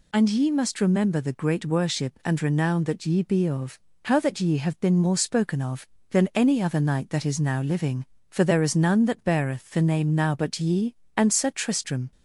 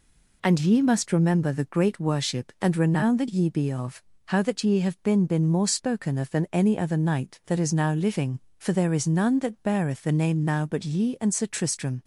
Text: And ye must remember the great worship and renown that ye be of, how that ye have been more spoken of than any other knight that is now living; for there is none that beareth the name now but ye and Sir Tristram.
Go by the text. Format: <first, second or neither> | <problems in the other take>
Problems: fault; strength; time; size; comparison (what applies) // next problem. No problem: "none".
first | says "been" twice; at 5.2 s